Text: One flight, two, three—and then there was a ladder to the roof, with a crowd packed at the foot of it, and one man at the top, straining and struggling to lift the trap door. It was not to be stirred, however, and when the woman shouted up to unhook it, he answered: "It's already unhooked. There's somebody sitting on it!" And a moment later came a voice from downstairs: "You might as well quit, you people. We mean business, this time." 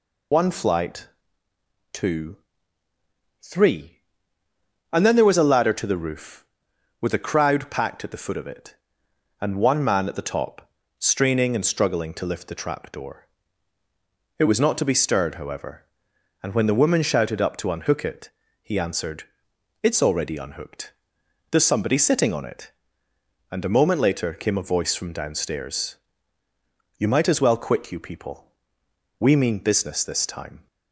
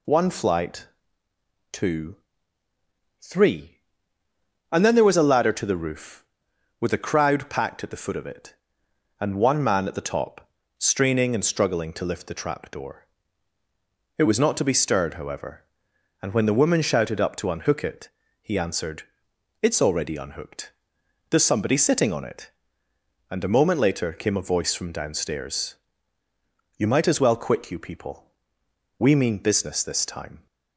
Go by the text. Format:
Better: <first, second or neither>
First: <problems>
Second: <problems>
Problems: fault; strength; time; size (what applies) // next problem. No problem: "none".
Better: second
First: loses the start of "One"; at 0.3 s; 50 ms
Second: none